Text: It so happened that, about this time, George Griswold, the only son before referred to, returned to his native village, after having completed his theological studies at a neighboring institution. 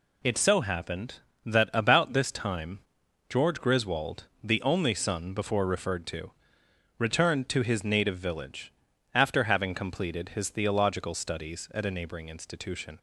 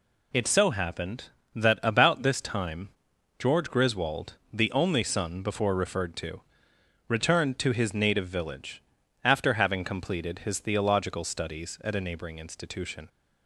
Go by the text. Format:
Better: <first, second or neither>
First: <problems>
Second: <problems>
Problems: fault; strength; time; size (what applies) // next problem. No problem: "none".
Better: neither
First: none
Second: none